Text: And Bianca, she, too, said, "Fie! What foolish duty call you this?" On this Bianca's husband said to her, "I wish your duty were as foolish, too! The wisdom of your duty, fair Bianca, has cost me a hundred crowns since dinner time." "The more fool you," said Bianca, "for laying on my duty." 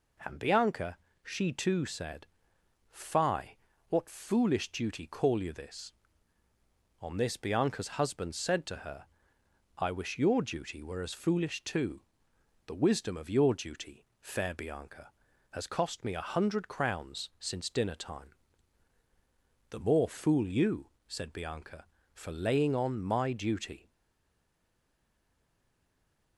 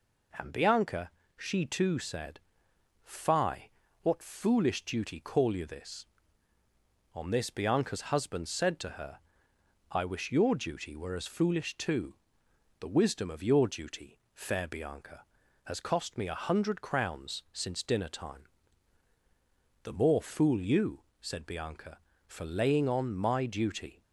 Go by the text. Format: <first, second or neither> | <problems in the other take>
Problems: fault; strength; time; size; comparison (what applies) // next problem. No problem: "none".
second | stays silent after the last word; strong; from 23.8 s on; 2.5 s long